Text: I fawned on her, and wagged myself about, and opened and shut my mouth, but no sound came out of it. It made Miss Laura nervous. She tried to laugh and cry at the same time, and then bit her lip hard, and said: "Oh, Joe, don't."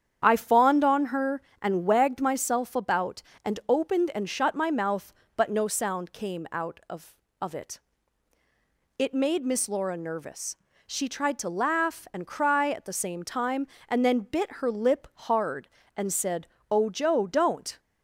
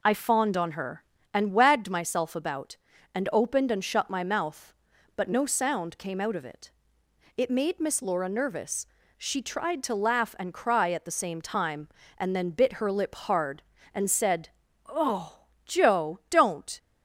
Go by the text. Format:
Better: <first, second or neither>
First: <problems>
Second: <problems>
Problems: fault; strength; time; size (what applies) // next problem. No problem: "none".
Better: second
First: starts louder than the rest; strong; until 1.2 s; 9 dB // says "of" twice; at 7.4 s // pauses between "lip" and "hard"; slight; at 15.0 s; 0.18 s long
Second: none